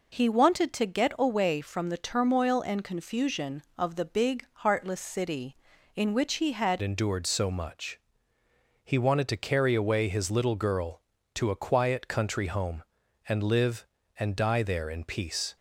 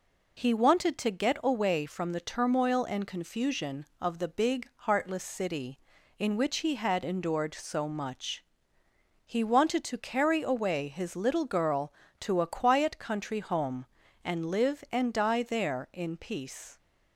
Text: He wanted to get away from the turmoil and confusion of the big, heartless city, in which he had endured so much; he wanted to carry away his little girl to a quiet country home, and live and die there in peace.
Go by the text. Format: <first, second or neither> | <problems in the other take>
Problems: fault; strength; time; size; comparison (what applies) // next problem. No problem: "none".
second | changes voice at "endured"; from 6.8 s on; 8.7 s long